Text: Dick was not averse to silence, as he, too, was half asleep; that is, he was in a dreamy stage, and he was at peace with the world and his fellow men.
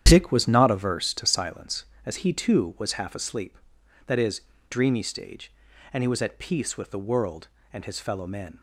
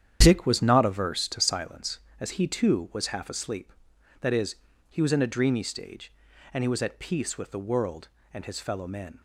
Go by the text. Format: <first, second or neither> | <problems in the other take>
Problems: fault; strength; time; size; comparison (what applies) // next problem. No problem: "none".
second | starts louder than the rest; strong; until 1.0 s; 10 dB; strong in the second // skips "he was in a"; at 4.5 s